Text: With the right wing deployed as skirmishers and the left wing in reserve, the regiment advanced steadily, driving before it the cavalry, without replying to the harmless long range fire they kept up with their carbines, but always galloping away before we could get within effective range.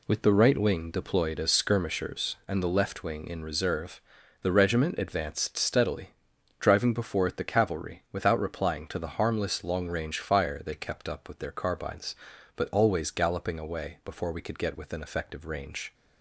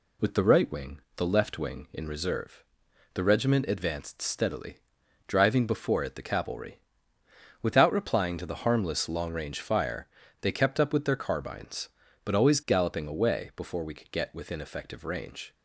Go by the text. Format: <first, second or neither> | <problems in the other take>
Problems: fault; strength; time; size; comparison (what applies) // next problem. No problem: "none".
first | skips "deployed as skirmishers and"; at 1.0 s // pauses between "fire" and "they"; slight; at 10.0 s; 0.34 s long